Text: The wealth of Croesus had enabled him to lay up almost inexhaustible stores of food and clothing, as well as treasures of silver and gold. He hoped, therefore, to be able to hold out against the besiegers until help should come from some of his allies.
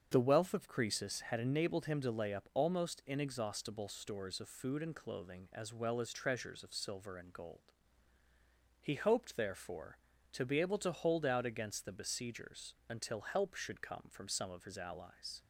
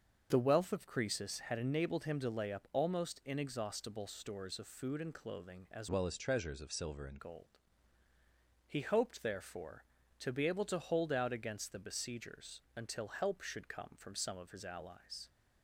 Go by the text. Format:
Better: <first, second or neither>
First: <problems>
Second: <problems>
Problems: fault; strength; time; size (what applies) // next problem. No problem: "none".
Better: first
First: starts louder than the rest; until 1.1 s; 7 dB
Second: starts louder than the rest; until 1.3 s; 6.5 dB // changes voice from "well" to "and"; from 5.8 to 7.1 s; 1.3 s long